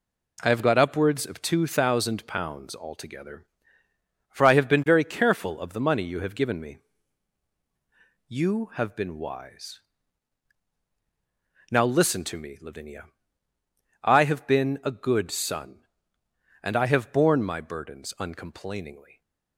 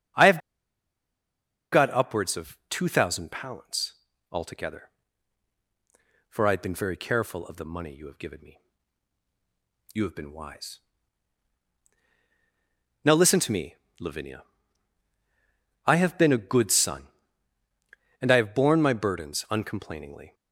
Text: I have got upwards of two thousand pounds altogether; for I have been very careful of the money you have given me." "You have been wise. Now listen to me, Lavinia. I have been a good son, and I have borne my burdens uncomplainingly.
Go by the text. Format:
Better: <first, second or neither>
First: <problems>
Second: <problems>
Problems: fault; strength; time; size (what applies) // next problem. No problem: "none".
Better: first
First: none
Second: starts louder than the rest; until 2.5 s; 6.5 dB // pauses between "have" and "got"; strong; at 0.3 s; 1.3 s long // pauses between "pounds" and "altogether"; at 3.9 s; 0.38 s long